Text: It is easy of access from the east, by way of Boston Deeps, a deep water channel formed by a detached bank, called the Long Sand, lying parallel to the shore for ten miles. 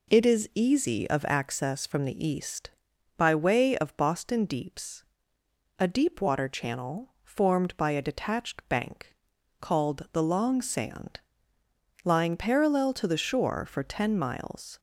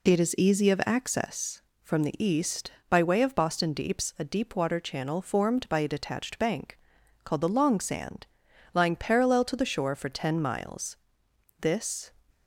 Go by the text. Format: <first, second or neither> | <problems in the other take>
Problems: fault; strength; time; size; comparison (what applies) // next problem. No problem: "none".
first | goes on to say "This"; from 11.5 s on; 0.54 s long